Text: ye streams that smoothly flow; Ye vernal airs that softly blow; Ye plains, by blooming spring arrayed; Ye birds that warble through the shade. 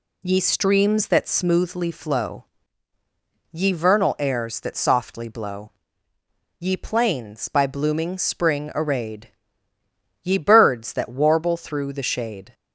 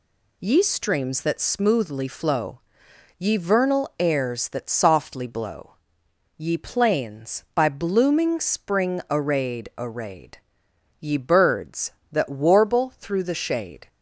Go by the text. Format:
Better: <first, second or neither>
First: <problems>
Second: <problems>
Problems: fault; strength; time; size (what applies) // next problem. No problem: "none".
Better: first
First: none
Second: says "arrayed" twice; at 9.7 s